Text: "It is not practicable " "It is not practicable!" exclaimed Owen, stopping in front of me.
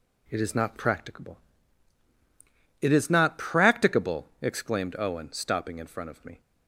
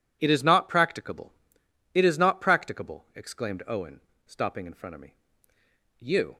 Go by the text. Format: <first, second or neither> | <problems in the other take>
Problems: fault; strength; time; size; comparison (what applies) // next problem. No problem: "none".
first | goes on to say "You"; slight; from 5.9 s on; 0.38 s long